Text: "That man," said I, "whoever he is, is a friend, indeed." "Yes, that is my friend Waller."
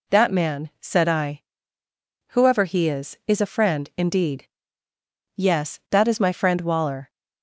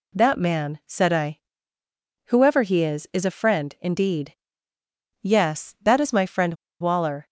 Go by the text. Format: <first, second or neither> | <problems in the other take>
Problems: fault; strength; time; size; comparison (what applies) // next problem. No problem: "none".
first | pauses between "friend" and "Waller"; slight; at 6.5 s; 0.27 s long